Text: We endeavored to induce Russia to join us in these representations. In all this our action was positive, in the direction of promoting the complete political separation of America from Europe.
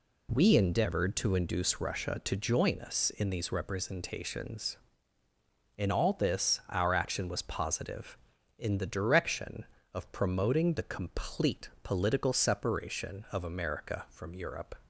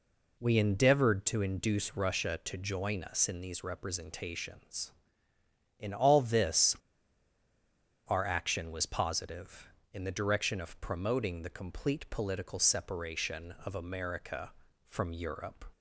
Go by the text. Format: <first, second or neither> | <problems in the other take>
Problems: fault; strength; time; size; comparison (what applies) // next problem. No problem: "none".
first | pauses between "this" and "our"; strong; at 6.7 s; 1.3 s long